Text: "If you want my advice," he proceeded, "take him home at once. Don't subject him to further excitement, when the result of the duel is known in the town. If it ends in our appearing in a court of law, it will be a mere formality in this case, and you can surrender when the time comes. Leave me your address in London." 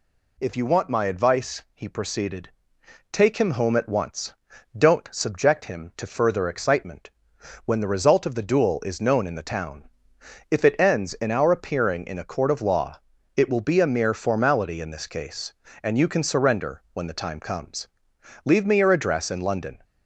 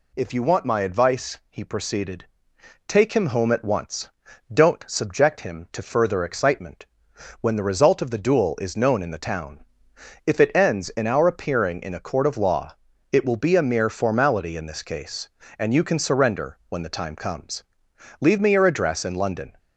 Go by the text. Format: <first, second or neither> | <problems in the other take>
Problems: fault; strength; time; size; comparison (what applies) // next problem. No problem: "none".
neither | none